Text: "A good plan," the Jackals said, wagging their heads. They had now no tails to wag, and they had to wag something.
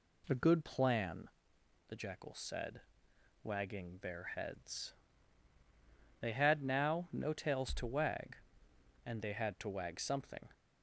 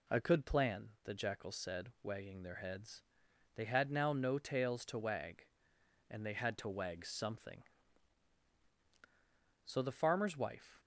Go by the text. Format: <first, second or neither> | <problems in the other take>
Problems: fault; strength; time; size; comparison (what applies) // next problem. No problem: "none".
first | goes on to say "So the Farmer's wife"; noticeable; from 9.6 s on; 1.1 s long